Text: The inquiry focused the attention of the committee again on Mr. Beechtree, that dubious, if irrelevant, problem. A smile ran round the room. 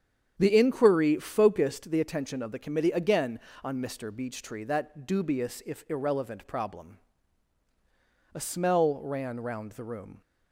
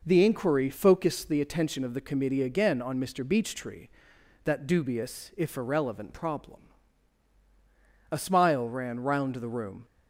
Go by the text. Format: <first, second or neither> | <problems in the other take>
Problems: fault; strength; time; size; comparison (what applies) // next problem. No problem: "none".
second | starts louder than the rest; strong; until 1.3 s; 8 dB // says "smell" for "smile"; at 8.4 s